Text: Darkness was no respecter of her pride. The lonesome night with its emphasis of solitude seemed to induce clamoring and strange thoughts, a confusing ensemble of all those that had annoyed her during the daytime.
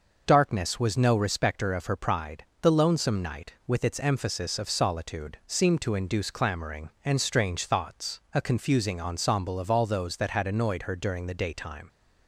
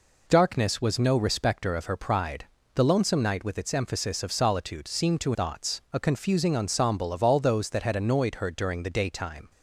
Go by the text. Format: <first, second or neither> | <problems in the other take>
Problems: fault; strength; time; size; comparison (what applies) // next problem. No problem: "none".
first | skips "induce clamoring and strange"; at 5.3 s